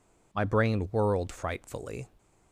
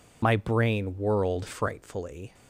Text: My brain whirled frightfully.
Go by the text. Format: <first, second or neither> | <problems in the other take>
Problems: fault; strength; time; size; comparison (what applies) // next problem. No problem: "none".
first | loses the start of "My"; at 0.2 s; 30 ms